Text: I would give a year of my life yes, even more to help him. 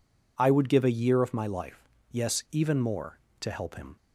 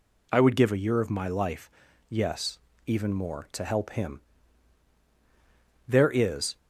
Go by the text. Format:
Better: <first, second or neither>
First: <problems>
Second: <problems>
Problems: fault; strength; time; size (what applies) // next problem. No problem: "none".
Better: first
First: pauses between "life" and "yes"; slight; at 1.8 s; 0.22 s long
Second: pauses between "life" and "yes"; at 1.7 s; 0.38 s long // goes on to say "There is"; noticeable; from 5.8 s on; 0.70 s long